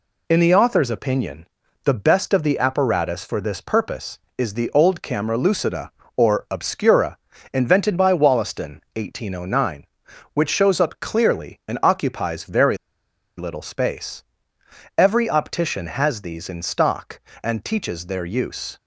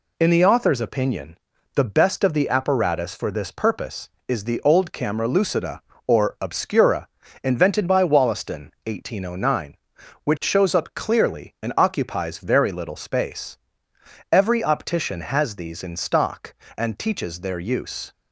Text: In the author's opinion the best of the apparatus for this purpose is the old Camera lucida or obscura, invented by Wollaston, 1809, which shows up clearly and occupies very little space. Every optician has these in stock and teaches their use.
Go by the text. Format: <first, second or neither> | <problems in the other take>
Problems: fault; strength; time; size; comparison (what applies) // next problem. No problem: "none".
second | pauses between "opinion" and "the"; at 1.4 s; 0.38 s long; also in the second // pauses between "very" and "little"; noticeable; at 12.7 s; 0.60 s long